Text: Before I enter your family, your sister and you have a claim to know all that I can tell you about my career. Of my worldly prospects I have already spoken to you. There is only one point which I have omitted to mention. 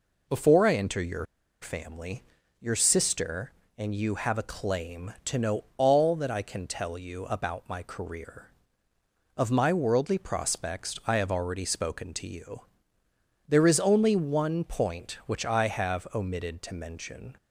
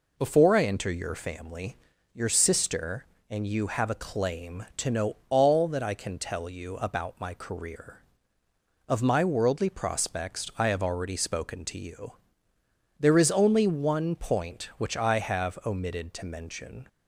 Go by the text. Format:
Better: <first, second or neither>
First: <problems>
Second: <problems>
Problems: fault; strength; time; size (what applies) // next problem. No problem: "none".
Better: second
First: pauses between "your" and "family"; at 1.2 s; 0.37 s long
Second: none